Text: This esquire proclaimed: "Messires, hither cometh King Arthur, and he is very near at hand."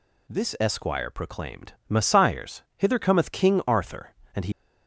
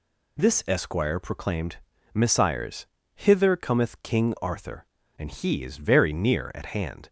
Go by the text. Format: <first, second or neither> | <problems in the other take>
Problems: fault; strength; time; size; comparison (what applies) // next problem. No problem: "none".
second | stops before "is very near at hand"; at 4.5 s